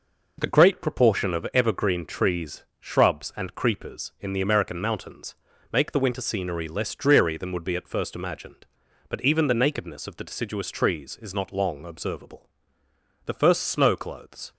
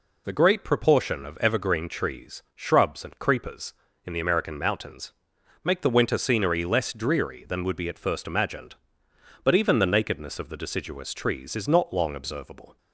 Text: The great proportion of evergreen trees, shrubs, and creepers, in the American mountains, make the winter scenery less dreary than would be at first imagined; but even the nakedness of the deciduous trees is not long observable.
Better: second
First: goes on to say "The first snow clothes"; noticeable; from 13.2 s on; 1.3 s long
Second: none

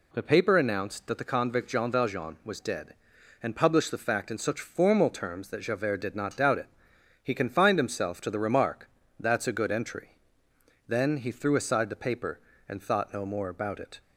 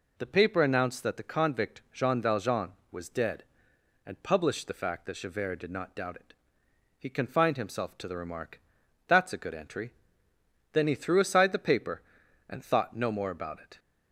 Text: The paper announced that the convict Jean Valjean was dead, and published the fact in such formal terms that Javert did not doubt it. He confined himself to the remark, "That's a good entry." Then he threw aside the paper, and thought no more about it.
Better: first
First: none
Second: skips "in such formal terms"; at 5.0 s

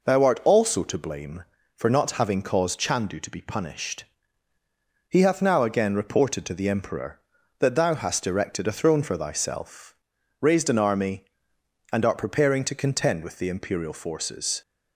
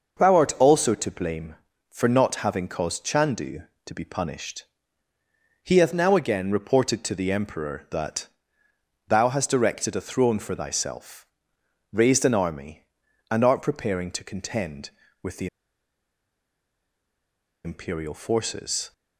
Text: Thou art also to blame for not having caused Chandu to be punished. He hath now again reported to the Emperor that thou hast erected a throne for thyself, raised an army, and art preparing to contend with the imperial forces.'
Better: first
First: none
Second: pauses between "that" and "thou"; noticeable; at 8.2 s; 0.82 s long // pauses between "the" and "imperial"; strong; at 15.4 s; 2.1 s long

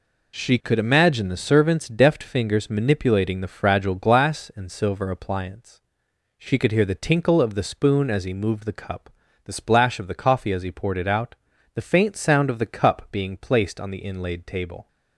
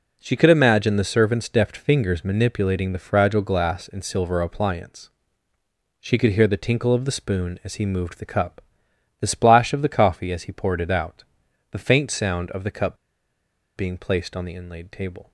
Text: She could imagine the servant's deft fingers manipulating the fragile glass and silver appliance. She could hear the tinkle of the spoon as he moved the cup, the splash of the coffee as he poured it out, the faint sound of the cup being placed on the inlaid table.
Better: first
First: none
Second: pauses between "cup" and "being"; noticeable; at 12.9 s; 0.80 s long

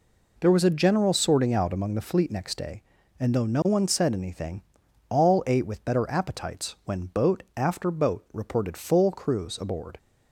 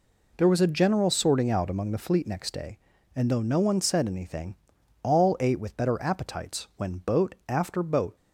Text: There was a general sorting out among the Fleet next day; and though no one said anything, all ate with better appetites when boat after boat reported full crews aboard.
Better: first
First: none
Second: stops before "reported full crews aboard"; at 8.1 s

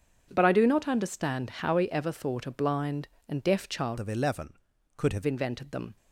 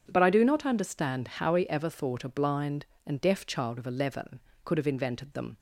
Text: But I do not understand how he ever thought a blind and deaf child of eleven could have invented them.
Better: second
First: starts louder than the rest; until 1.3 s; 7 dB // changes voice from "of" to "have"; from 3.9 to 5.2 s; 1.3 s long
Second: starts louder than the rest; strong; until 1.0 s; 7.5 dB

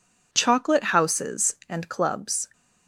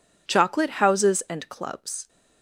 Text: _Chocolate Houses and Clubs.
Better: neither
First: none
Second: none

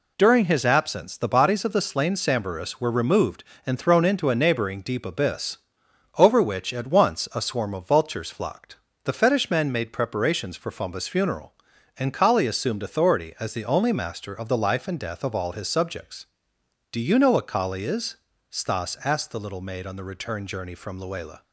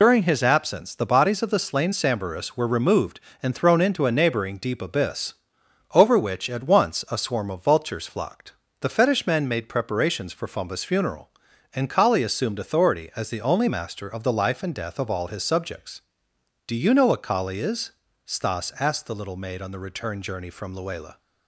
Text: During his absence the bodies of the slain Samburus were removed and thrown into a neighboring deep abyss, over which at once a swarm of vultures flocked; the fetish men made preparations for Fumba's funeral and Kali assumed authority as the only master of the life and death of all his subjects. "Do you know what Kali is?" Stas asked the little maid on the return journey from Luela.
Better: first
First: none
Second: loses the start of "During"; at 0.0 s; 65 ms

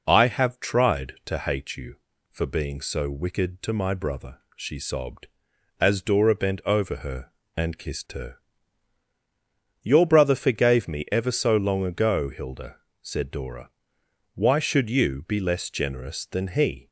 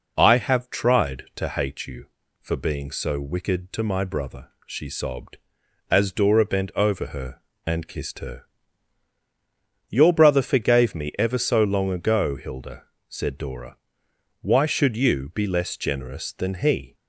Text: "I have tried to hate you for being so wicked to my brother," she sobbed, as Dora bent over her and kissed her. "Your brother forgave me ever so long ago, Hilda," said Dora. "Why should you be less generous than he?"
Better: neither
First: none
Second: none

